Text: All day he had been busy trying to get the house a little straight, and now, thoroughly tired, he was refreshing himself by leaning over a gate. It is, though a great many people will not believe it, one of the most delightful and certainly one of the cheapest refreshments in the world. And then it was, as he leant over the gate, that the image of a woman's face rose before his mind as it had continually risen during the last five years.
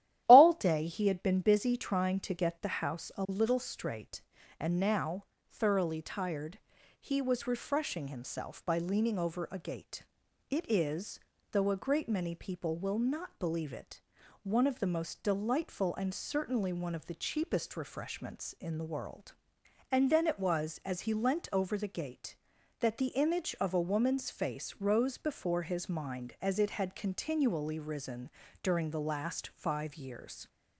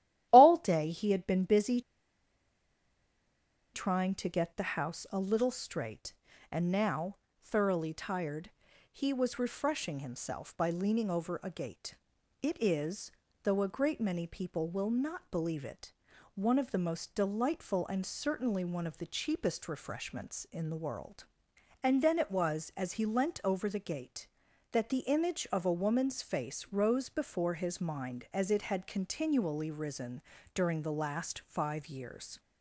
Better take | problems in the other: first | starts louder than the rest; strong; until 1.3 s; 12.5 dB; strong in the first // pauses between "busy" and "trying"; strong; at 1.7 s; 1.9 s long // pauses between "risen" and "during"; slight; at 30.2 s; 0.32 s long; slight in the first

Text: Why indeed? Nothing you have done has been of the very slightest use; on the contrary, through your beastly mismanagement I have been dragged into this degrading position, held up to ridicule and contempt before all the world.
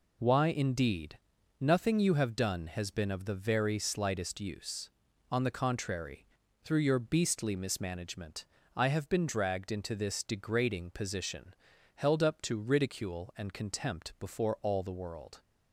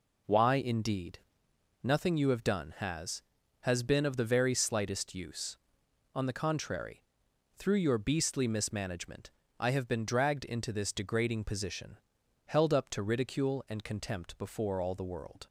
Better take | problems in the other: first | says "has" twice; at 3.6 s // pauses between "mismanagement" and "I"; slight; at 9.2 s; 0.32 s long; slight in the first

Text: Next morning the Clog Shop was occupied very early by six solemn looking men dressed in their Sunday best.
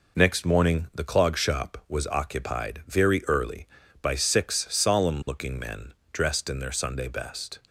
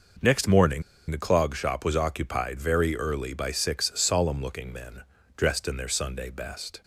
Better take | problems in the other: first | pauses between "morning" and "the"; slight; at 0.8 s; 0.28 s long // pauses between "men" and "dressed"; slight; at 5.0 s; 0.34 s long; slight in the first

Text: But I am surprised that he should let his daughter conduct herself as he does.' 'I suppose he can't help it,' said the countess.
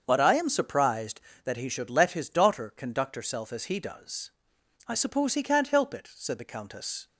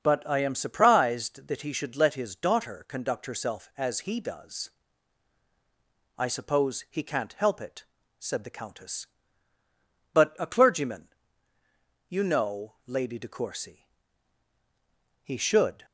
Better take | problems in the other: first | starts louder than the rest; until 1.0 s; 6.5 dB; also in the first // goes on to say "But a clergyman you know Lady De Courcy He should"; strong; from 10.1 s on; 5.7 s long

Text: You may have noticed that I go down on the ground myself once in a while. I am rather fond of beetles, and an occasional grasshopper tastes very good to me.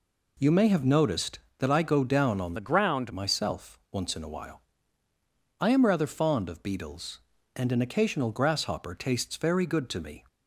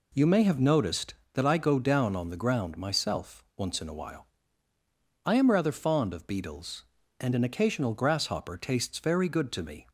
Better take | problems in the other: second | changes voice from "the" to "ground"; from 2.5 to 3.1 s; 0.6 s long

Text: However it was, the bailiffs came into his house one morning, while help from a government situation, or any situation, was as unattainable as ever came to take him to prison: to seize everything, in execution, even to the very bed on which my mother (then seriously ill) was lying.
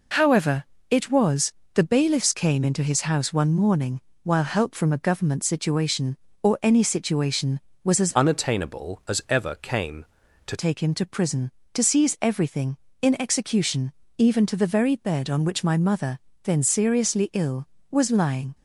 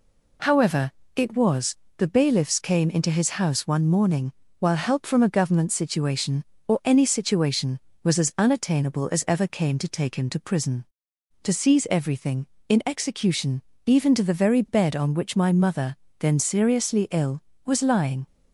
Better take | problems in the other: second | pauses between "However" and "it"; slight; at 0.6 s; 0.24 s long; slight in the second // changes voice from "unattainable" to "to"; from 8.1 to 10.5 s; 2.4 s long

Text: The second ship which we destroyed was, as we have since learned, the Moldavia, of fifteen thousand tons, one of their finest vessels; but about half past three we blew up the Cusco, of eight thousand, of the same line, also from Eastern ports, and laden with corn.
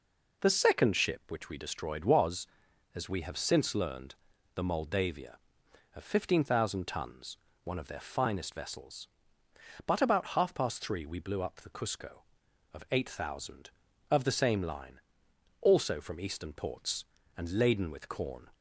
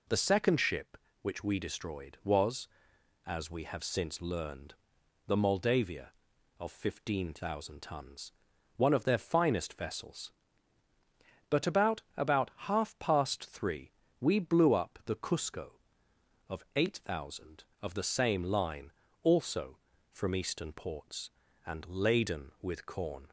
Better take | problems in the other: first | says "about" twice; at 12.1 s // pauses between "three" and "we"; slight; at 13.9 s; 0.30 s long

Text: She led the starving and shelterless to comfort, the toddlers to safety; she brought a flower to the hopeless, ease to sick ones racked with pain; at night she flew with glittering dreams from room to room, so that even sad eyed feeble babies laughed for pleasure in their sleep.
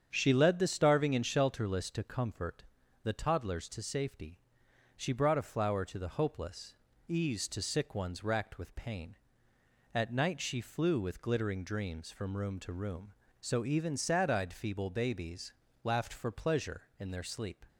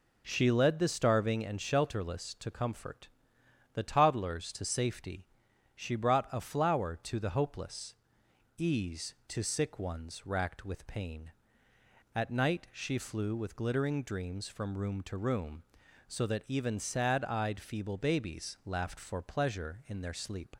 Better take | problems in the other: second | starts louder than the rest; strong; until 1.1 s; 8 dB // skips "that"; at 13.6 s // pauses between "babies" and "laughed"; slight; at 15.5 s; 0.28 s long

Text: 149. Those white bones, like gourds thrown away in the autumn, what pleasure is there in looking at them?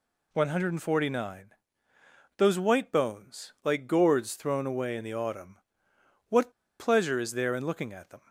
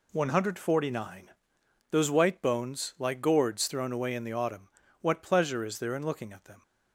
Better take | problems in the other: second | pauses between "what" and "pleasure"; slight; at 6.5 s; 0.27 s long

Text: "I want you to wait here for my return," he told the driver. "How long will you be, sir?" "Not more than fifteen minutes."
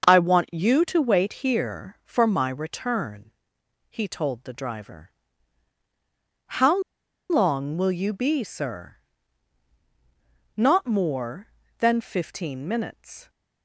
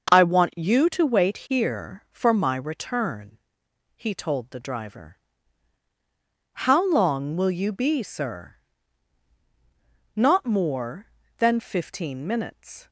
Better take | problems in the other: second | starts louder than the rest; until 1.0 s; 6.5 dB; also in the second // pauses between "How" and "long"; noticeable; at 6.8 s; 0.49 s long

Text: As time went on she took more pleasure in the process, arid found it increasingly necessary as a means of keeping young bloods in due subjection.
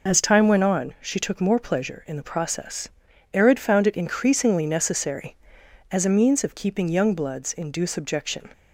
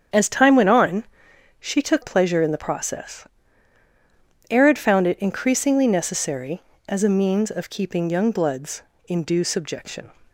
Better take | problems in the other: first | starts louder than the rest; strong; until 1.7 s; 8 dB // pauses between "on" and "she"; noticeable; at 1.0 s; 0.56 s long // skips "more"; at 2.0 s

